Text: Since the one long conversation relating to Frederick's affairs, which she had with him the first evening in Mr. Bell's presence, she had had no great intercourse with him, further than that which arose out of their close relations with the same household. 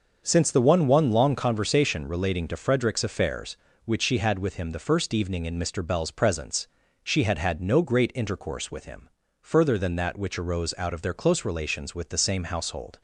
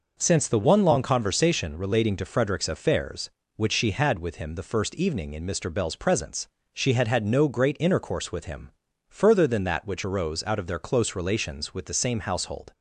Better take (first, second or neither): second